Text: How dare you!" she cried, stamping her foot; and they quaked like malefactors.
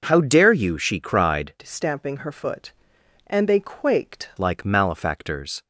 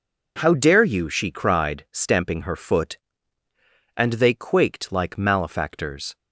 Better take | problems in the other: second | changes voice from "stamping" to "quaked"; from 1.6 to 4.2 s; 2.6 s long

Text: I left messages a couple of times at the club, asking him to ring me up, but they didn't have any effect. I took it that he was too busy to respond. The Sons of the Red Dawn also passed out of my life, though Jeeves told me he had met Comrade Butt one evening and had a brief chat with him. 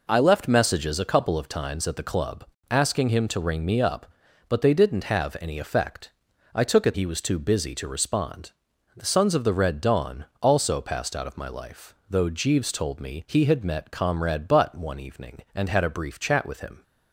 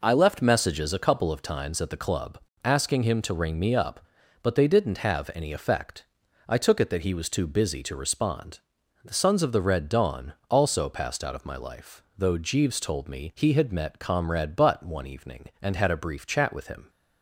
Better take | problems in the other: second | skips "that"; at 6.9 s // pauses between "Dawn" and "also"; slight; at 10.2 s; 0.16 s long; slight in the second

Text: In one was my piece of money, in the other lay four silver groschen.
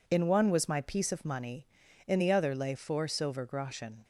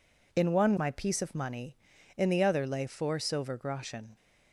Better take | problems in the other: first | skips "was"; at 0.7 s

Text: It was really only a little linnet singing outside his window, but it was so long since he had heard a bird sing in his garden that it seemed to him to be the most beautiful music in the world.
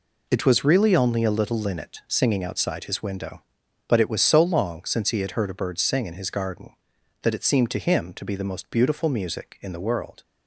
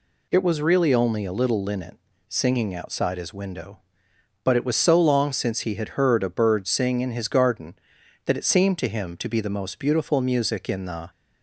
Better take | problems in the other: first | pauses between "linnet" and "singing"; slight; at 1.9 s; 0.30 s long // stops before "world"; at 11.0 s

